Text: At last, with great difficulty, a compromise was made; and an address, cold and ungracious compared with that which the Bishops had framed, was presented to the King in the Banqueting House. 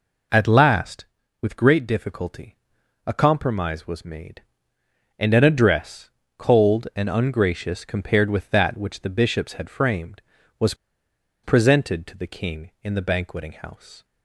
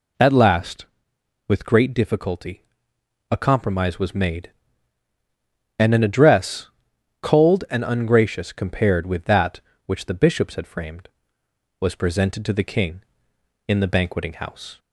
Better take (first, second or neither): second